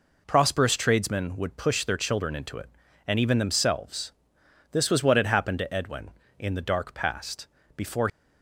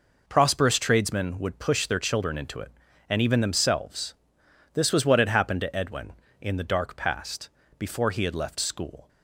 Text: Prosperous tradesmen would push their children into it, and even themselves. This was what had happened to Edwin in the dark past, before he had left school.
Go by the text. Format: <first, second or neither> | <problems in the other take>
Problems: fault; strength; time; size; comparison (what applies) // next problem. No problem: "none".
second | stops before "he had left school"; at 8.0 s